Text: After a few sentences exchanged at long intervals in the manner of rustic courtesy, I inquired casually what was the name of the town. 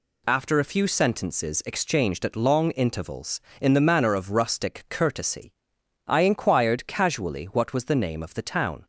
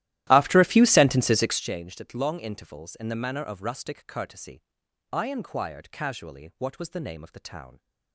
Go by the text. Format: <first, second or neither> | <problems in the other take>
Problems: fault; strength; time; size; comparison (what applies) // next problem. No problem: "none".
first | starts louder than the rest; strong; until 1.7 s; 14.5 dB